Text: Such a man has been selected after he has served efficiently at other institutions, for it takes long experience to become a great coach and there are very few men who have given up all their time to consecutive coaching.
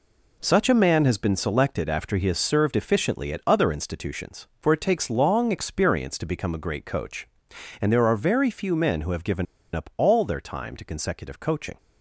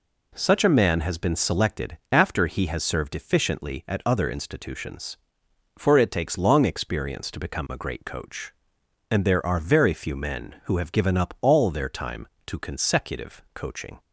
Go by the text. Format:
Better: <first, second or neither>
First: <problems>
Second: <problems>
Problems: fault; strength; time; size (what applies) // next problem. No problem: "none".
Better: second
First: pauses between "given" and "up"; slight; at 9.4 s; 0.29 s long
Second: none